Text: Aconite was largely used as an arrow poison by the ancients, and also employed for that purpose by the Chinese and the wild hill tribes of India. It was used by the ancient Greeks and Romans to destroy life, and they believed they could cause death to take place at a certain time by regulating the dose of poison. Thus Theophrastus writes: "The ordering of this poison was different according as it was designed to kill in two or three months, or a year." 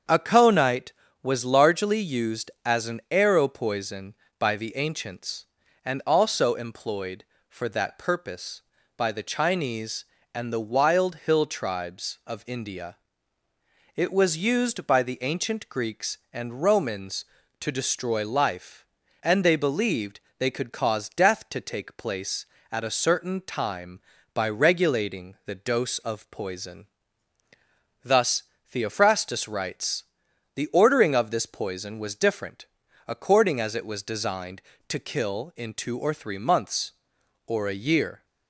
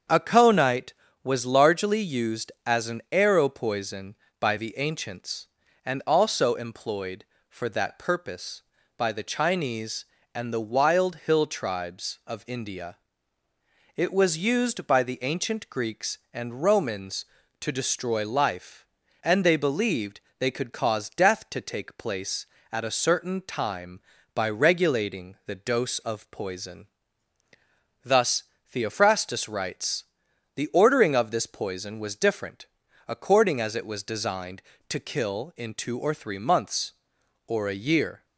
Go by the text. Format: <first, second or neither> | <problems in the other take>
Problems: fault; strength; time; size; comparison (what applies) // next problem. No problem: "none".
neither | starts louder than the rest; strong; the same in both // pauses between "believed" and "they"; slight; the same in both // pauses between "Thus" and "Theophrastus"; slight; the same in both // pauses between "different" and "according"; the same in both